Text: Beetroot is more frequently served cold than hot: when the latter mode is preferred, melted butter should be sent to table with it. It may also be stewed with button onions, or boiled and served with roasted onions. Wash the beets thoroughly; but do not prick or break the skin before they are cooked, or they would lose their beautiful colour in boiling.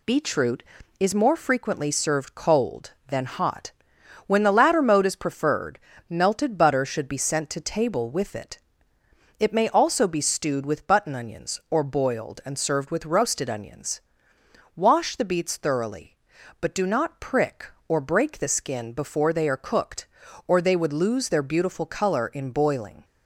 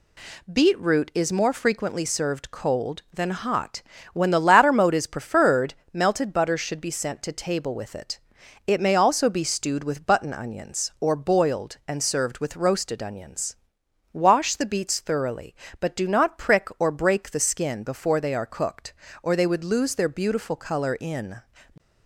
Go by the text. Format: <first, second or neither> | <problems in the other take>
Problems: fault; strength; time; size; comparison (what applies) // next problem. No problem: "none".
first | stops before "boiling"; at 21.7 s